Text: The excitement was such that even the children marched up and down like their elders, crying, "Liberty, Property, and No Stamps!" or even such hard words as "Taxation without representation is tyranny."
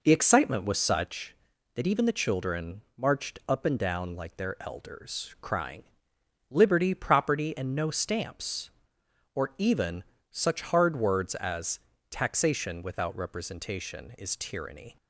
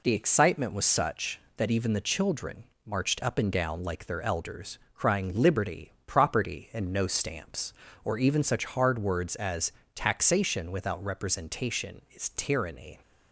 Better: second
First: starts louder than the rest; noticeable; until 1.2 s; 5 dB // pauses between "children" and "marched"; slight; at 2.8 s; 0.16 s long // pauses between "even" and "such"; slight; at 10.0 s; 0.28 s long // pauses between "as" and "Taxation"; slight; at 11.8 s; 0.28 s long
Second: pauses between "children" and "marched"; slight; at 2.6 s; 0.22 s long // pauses between "as" and "Taxation"; slight; at 9.7 s; 0.22 s long

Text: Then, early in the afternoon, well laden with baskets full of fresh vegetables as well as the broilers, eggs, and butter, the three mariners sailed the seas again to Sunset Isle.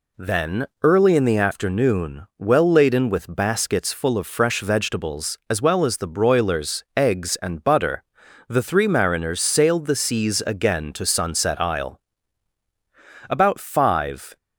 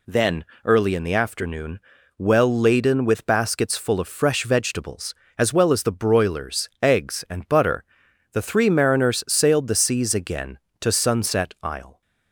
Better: second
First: goes on to say "About five"; noticeable; from 13.2 s on; 1.0 s long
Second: none

